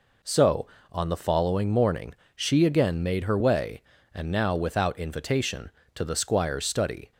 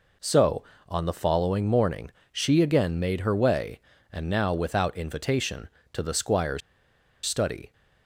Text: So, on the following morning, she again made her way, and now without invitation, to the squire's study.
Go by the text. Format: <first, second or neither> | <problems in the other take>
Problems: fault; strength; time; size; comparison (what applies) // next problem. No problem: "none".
first | pauses between "squire's" and "study"; noticeable; at 6.6 s; 0.65 s long